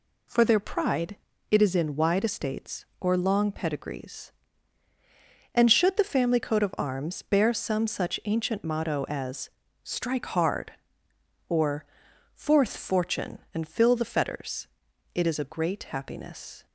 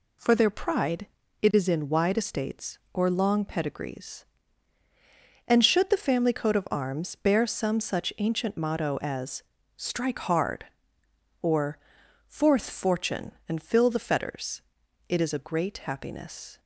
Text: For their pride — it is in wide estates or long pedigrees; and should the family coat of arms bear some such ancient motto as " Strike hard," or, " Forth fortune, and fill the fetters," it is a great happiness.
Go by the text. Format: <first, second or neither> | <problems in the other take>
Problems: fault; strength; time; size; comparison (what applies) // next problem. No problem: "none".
neither | none